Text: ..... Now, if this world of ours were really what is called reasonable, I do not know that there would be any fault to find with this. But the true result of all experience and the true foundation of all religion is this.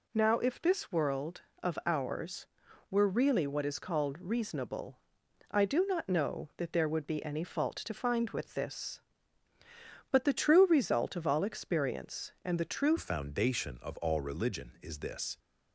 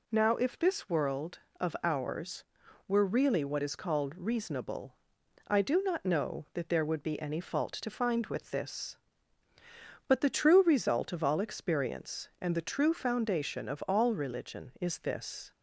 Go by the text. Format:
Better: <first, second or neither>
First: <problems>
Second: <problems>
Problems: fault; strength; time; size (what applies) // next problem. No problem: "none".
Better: second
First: changes voice at "foundation"; from 12.9 s on; 2.4 s long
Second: none